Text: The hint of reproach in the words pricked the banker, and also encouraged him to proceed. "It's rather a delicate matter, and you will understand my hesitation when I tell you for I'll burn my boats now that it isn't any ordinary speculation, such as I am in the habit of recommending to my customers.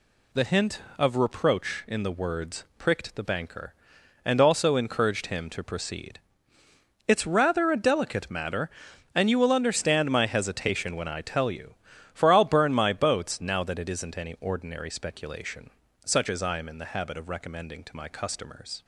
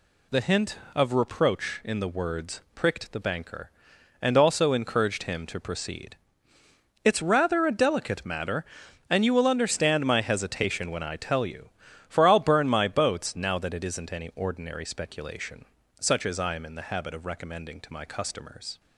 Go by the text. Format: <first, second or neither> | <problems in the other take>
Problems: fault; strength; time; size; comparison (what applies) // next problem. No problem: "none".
neither | none